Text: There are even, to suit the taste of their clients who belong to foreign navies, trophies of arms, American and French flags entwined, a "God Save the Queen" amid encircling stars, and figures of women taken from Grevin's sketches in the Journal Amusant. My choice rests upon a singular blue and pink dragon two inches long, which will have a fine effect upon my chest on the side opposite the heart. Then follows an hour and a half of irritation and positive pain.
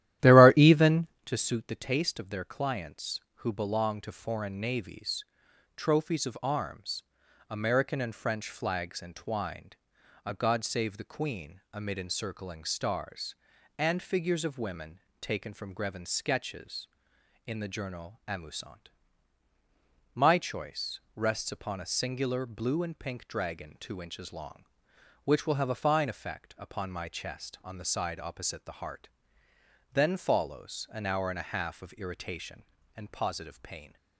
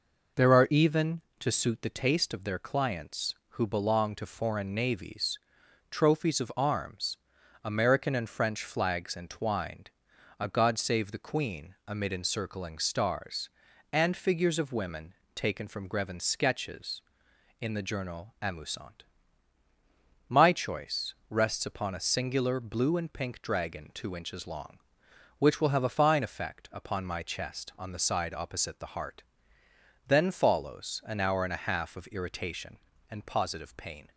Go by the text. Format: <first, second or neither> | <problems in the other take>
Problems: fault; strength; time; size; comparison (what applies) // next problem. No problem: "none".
second | starts louder than the rest; strong; until 1.3 s; 13 dB // pauses between "women" and "taken"; slight; at 14.9 s; 0.20 s long; slight in the second